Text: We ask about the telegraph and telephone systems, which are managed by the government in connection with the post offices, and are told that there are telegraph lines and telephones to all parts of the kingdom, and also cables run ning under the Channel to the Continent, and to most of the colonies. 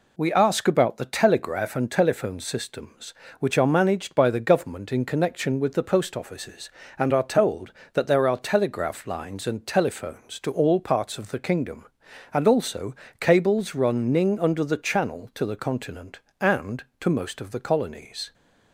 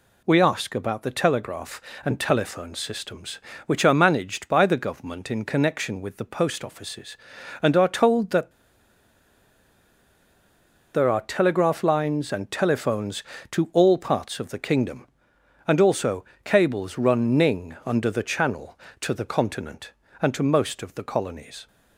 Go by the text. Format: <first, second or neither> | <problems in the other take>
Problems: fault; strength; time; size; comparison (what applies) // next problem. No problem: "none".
first | pauses between "that" and "there"; strong; at 8.5 s; 2.4 s long // pauses between "also" and "cables"; slight; at 16.2 s; 0.22 s long; slight in the first